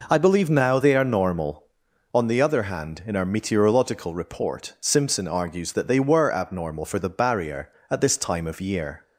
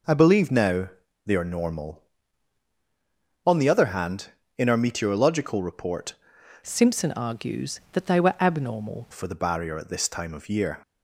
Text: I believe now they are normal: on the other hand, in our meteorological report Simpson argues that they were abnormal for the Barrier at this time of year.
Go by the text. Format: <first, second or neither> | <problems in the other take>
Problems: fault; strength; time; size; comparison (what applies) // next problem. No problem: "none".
first | pauses between "now" and "they"; slight; at 0.8 s; 0.34 s long // changes voice from "Simpson" to "abnormal"; from 6.6 to 9.0 s; 2.4 s long